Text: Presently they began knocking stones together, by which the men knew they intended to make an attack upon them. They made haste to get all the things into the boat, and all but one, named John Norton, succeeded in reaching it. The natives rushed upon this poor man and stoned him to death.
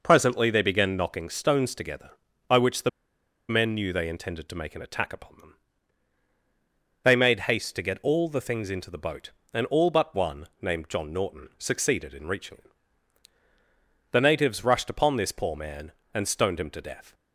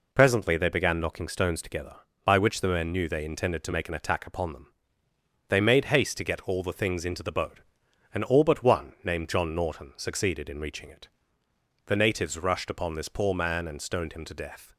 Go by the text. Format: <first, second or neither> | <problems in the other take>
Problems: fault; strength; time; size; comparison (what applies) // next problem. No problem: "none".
second | pauses between "the" and "men"; noticeable; at 2.8 s; 0.59 s long